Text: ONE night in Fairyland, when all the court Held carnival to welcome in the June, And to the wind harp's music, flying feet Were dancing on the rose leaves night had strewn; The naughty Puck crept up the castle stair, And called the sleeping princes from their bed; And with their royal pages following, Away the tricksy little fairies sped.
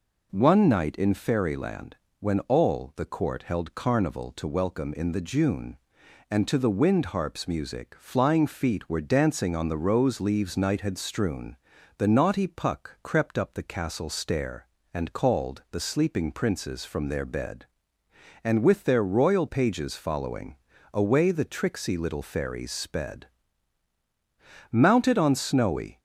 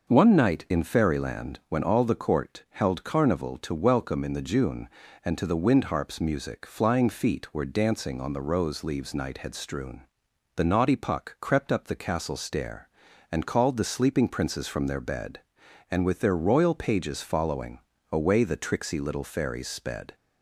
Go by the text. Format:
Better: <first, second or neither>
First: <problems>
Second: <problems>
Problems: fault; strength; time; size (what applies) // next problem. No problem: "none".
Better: second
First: goes on to say "Mounted on snowy"; noticeable; from 24.7 s on; 1.2 s long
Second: none